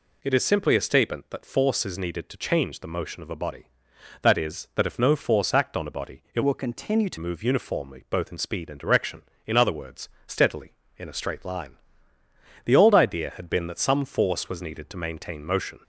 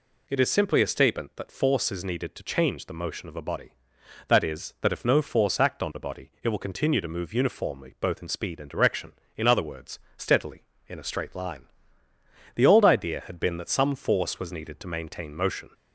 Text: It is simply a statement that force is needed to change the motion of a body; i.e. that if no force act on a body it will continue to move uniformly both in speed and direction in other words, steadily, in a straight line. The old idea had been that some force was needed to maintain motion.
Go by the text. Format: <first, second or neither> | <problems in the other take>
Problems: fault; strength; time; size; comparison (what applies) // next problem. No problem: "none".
second | changes voice from "will" to "to"; from 6.4 to 7.1 s; 0.7 s long